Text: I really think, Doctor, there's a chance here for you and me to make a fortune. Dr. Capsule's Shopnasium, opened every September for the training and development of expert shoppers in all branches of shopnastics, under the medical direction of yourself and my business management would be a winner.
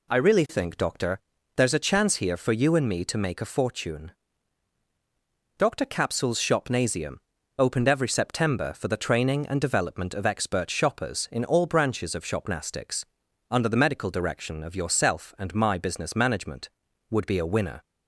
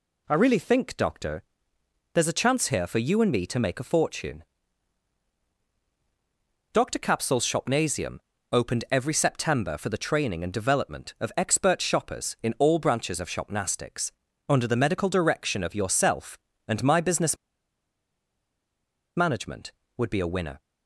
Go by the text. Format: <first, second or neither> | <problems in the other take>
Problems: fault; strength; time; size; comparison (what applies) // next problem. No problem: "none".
first | pauses between "business" and "management"; strong; at 17.3 s; 1.8 s long